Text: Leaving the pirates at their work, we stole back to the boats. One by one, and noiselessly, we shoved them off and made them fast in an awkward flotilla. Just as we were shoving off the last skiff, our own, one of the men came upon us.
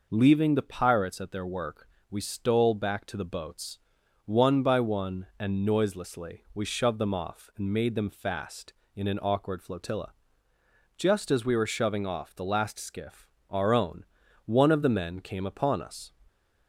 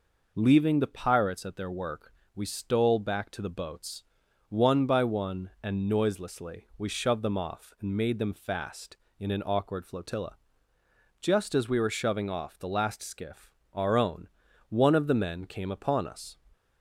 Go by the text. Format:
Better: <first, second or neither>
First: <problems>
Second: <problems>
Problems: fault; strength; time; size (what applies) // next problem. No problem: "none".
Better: neither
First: none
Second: none